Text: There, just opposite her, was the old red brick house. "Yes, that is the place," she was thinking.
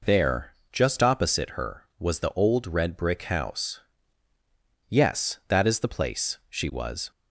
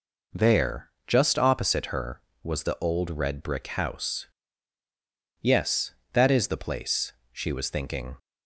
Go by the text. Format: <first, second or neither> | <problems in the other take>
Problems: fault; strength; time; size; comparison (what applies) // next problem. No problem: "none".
second | stops before "thinking"; at 7.1 s